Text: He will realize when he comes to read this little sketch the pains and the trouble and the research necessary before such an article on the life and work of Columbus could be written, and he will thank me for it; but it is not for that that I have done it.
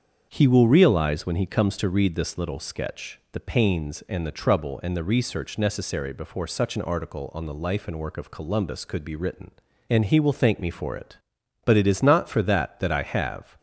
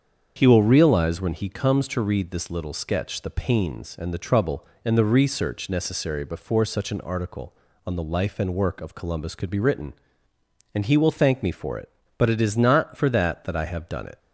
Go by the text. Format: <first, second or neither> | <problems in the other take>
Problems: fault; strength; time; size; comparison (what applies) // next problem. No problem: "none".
second | starts louder than the rest; until 1.3 s; 7 dB; also in the second // stops before "done it"; at 13.5 s